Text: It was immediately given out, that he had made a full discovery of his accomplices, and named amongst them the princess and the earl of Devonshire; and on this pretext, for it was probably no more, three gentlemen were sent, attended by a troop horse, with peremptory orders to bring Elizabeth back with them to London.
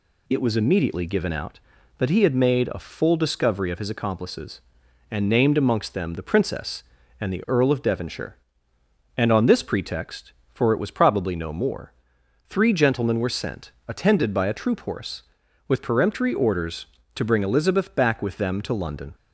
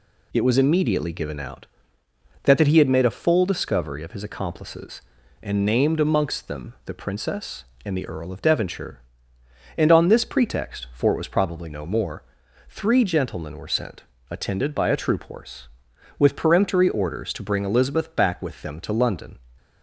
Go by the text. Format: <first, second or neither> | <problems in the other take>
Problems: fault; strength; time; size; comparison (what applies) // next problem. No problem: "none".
first | says "that" twice; at 2.5 s